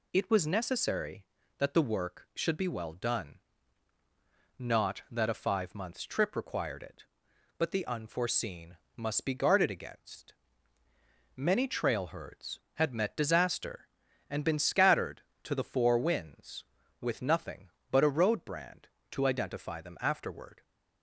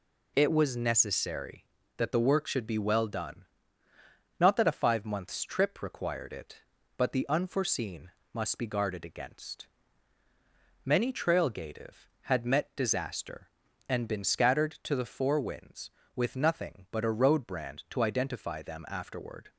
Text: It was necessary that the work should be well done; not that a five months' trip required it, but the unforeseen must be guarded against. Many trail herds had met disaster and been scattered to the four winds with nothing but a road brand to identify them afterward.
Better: first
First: pauses between "unforeseen" and "must"; slight; at 8.7 s; 0.20 s long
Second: pauses between "unforeseen" and "must"; slight; at 8.0 s; 0.22 s long // says "gative" for "herds"; at 11.4 s

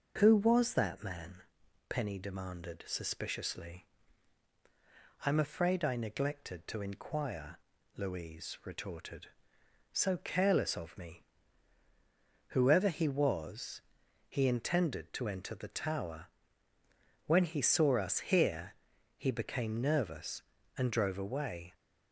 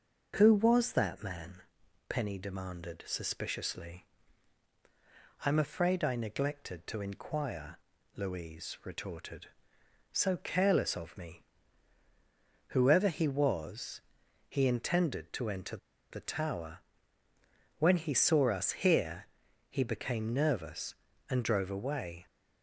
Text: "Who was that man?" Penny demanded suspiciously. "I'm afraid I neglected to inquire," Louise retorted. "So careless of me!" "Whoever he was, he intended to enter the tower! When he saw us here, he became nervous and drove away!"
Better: first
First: none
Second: pauses between "enter" and "the"; slight; at 15.7 s; 0.33 s long

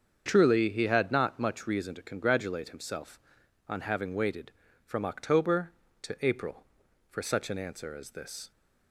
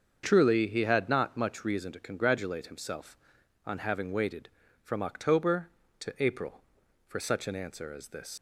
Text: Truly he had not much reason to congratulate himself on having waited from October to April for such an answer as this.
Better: first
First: starts louder than the rest; strong; until 1.2 s; 7 dB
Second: starts louder than the rest; until 1.2 s; 7 dB // leaves "this" unfinished; at 8.3 s; 105 ms

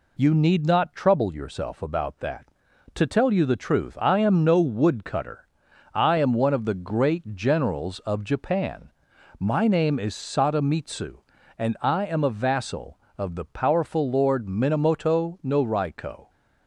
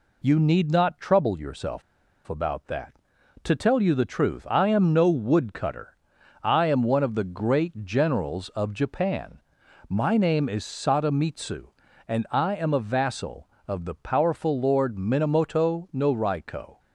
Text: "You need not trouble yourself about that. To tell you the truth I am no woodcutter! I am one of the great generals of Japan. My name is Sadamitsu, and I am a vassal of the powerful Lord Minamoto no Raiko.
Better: first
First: none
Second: pauses between "yourself" and "about"; at 1.8 s; 0.44 s long

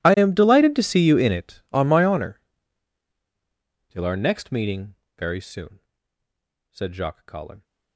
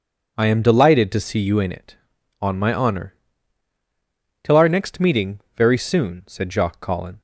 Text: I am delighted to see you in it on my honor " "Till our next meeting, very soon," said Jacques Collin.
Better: second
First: gets quieter; strong; throughout; 24.5 dB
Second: none

